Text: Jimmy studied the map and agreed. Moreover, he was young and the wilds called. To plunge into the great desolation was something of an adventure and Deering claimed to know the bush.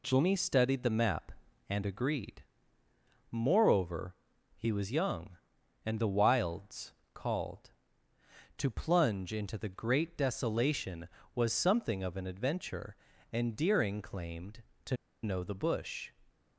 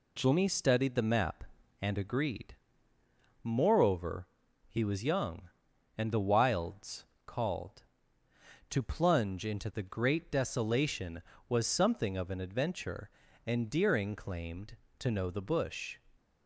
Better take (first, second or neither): second